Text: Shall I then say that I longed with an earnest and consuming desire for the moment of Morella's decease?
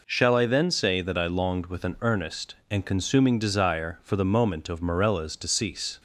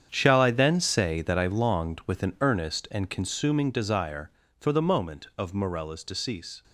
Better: first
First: none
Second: gets quieter; strong; throughout; 12.5 dB

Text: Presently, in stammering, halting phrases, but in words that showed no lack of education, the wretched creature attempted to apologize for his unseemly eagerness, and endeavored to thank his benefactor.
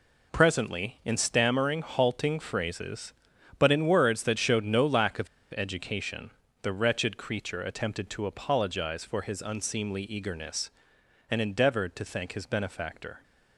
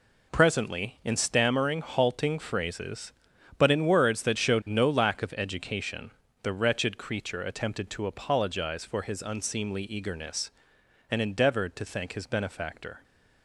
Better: second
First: pauses between "of" and "education"; slight; at 5.2 s; 0.26 s long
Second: none

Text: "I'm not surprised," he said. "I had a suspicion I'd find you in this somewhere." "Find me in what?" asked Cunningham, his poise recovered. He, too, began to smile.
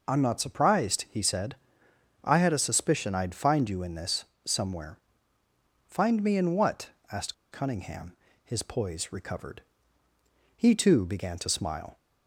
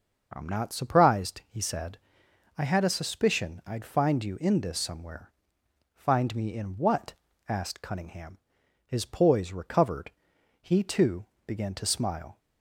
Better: second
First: pauses between "this" and "somewhere"; slight; at 4.2 s; 0.20 s long // pauses between "asked" and "Cunningham"; slight; at 7.3 s; 0.17 s long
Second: none

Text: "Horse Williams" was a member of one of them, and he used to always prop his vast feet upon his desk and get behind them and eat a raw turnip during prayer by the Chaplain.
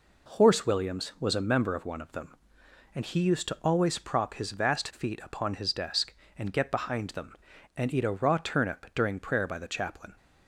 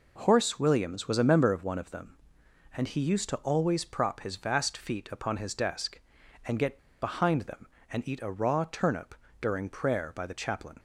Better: first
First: none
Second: pauses between "get" and "behind"; slight; at 6.7 s; 0.23 s long // pauses between "turnip" and "during"; slight; at 9.1 s; 0.26 s long

